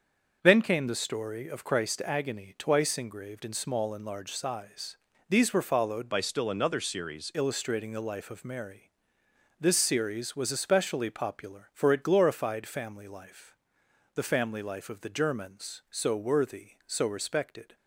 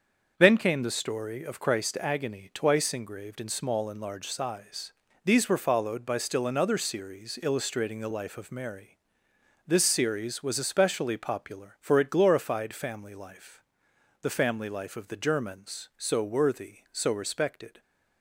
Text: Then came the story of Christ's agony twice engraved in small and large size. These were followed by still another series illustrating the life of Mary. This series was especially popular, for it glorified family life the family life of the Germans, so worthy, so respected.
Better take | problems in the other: second | starts louder than the rest; until 1.4 s; 6.5 dB; also in the second // changes voice from "by" to "series"; from 6.1 to 7.3 s; 1.2 s long // pauses between "life" and "the"; noticeable; at 13.5 s; 0.62 s long; noticeable in the second

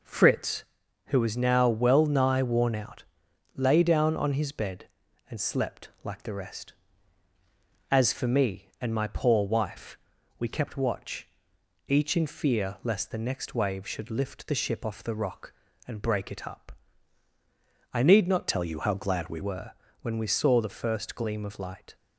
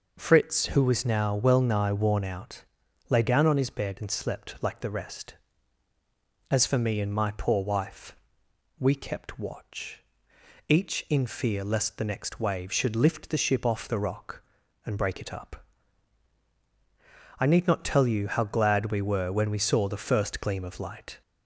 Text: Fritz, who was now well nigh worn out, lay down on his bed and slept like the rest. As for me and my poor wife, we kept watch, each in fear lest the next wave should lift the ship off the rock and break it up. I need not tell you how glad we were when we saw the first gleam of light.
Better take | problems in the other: second | changes voice from "tell" to "we"; from 18.4 to 19.3 s; 0.9 s long // pauses between "were" and "when"; slight; at 19.7 s; 0.28 s long

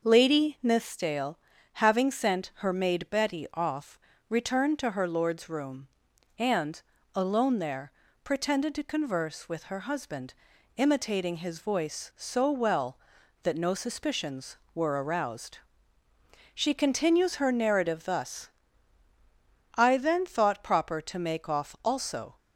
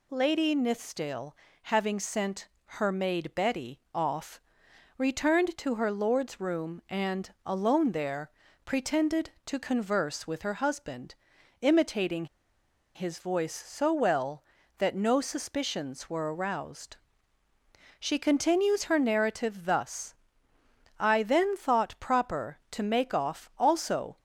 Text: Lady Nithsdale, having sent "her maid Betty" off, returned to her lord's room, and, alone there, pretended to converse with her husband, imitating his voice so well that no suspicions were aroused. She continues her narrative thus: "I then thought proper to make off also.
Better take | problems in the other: first | pauses between "sent" and "her"; slight; at 2.4 s; 0.18 s long // pauses between "imitating" and "his"; noticeable; at 12.2 s; 0.69 s long

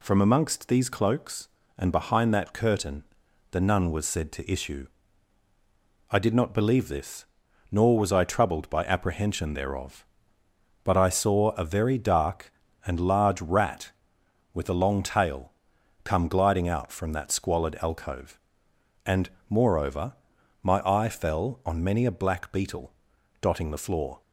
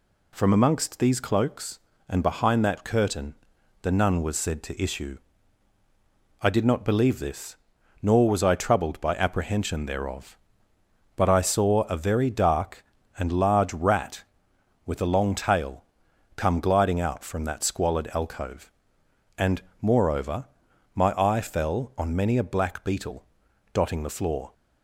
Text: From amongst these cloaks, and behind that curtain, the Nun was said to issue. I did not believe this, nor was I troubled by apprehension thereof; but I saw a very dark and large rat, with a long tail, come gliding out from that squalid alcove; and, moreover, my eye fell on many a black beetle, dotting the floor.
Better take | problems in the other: neither | none

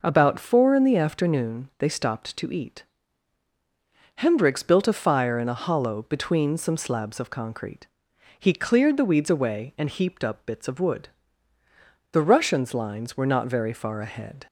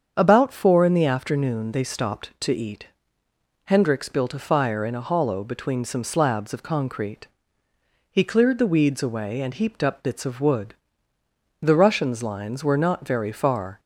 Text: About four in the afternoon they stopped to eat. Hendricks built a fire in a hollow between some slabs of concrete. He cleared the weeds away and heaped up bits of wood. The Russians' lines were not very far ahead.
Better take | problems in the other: first | starts louder than the rest; strong; until 1.1 s; 7.5 dB // stops before "ahead"; at 13.7 s

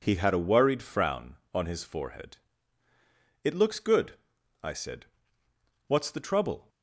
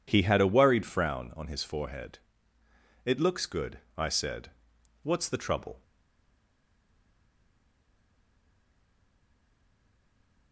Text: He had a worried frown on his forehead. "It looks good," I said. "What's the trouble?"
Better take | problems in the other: first | stays silent after the last word; strong; from 5.8 s on; 4.7 s long

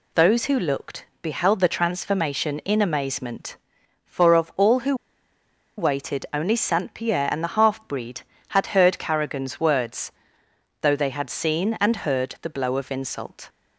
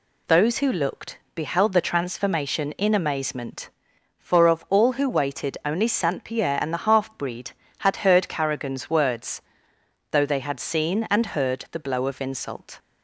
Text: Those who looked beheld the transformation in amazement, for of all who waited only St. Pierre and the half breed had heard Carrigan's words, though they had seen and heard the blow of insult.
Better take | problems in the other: second | pauses between "looked" and "beheld"; slight; at 1.0 s; 0.16 s long; slight in the second // pauses between "who" and "waited"; noticeable; at 4.9 s; 0.83 s long

